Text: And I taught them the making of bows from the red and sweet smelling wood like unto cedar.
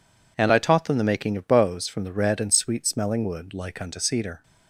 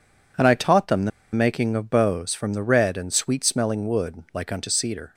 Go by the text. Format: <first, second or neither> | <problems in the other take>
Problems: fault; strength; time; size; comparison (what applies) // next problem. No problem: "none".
first | pauses between "the" and "making"; slight; at 1.1 s; 0.23 s long